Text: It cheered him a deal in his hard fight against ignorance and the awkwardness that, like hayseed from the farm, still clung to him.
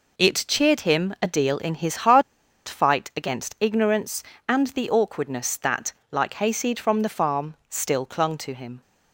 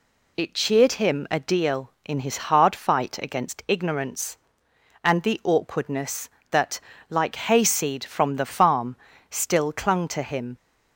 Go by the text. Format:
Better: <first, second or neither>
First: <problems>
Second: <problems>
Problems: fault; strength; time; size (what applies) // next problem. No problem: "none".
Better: second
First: pauses between "hard" and "fight"; at 2.2 s; 0.45 s long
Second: none